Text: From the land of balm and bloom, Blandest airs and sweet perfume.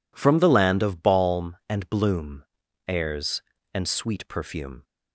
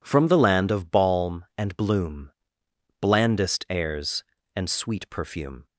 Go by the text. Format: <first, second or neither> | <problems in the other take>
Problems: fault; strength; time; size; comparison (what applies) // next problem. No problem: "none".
second | skips "Blandest"; at 2.6 s